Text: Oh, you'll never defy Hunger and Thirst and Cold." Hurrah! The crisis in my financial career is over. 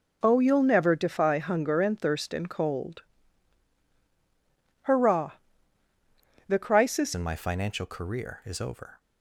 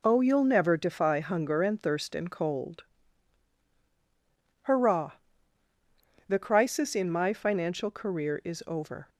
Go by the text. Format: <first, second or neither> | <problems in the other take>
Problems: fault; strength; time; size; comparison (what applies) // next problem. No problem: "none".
second | changes voice at "in"; from 7.1 s on; 1.8 s long